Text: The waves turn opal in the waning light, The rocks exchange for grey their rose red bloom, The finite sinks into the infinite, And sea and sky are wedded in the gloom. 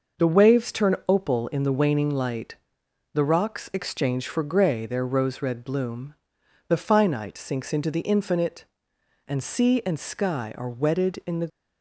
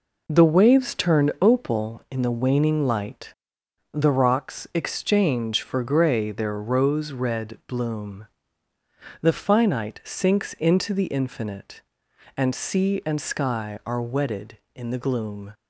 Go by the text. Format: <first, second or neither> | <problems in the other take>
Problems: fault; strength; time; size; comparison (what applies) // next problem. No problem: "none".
second | stops before "gloom"; at 11.4 s